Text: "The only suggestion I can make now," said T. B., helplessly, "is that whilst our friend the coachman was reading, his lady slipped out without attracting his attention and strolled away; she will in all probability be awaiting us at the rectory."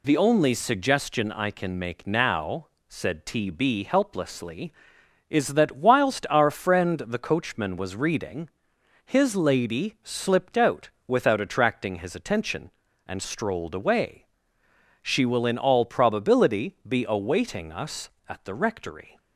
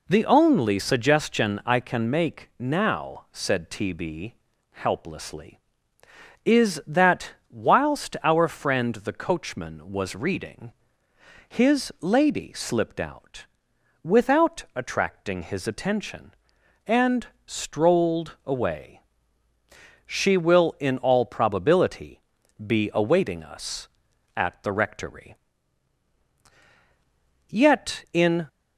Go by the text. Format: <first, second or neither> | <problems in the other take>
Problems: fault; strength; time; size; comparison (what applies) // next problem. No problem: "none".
first | pauses between "that" and "whilst"; slight; at 7.3 s; 0.16 s long // pauses between "out" and "without"; noticeable; at 13.4 s; 0.54 s long; slight in the first // pauses between "and" and "strolled"; slight; at 17.2 s; 0.18 s long // pauses between "probability" and "be"; at 22.2 s; 0.44 s long // goes on to say "Yet in"; noticeable; from 27.4 s on; 0.98 s long